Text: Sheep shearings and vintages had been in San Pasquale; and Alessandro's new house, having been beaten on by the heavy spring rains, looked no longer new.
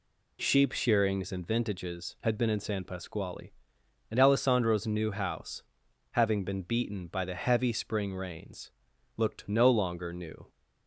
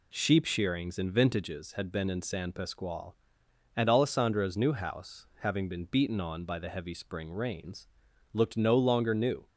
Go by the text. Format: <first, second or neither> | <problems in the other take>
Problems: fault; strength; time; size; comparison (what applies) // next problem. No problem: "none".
second | skips "on"; at 7.0 s